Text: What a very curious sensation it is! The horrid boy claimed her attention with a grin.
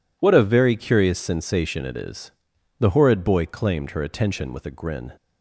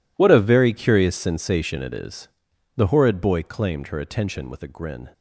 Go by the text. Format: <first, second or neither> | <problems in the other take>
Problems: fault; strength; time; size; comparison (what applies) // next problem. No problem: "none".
first | gets quieter; strong; throughout; 16 dB